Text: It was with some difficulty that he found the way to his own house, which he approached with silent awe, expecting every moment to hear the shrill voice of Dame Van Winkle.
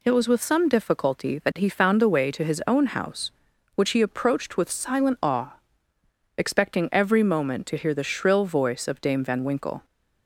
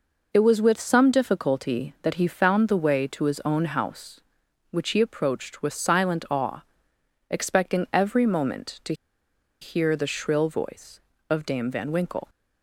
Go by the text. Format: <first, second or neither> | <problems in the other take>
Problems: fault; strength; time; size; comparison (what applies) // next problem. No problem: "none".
first | pauses between "to" and "hear"; noticeable; at 8.9 s; 0.67 s long